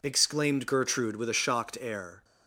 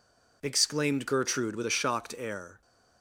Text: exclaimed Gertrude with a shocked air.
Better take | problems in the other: neither | none

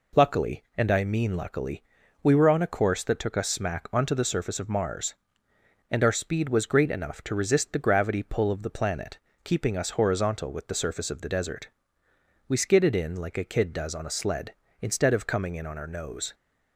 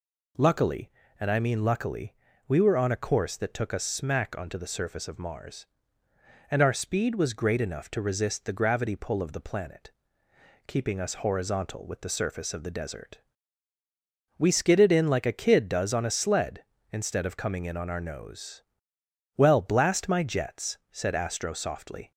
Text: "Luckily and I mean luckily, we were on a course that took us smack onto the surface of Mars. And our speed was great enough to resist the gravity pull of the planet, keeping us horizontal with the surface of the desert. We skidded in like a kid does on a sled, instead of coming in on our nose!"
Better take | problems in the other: first | goes on to say "Well blast my jets said Astro softly"; strong; from 19.3 s on; 2.7 s long

